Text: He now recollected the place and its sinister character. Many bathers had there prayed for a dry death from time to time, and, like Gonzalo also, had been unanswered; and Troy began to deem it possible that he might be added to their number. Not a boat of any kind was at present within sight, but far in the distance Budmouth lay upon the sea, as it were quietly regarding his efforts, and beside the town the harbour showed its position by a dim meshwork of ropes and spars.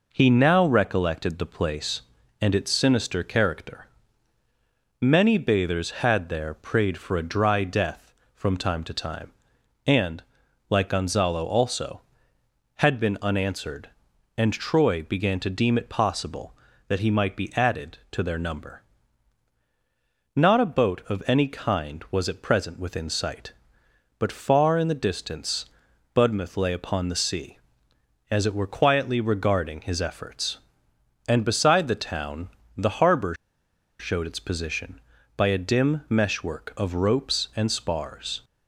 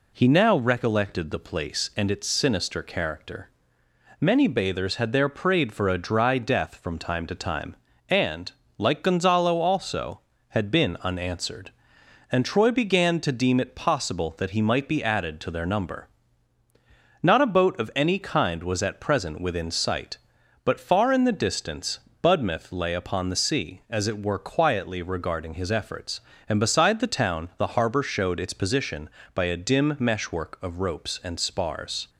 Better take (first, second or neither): second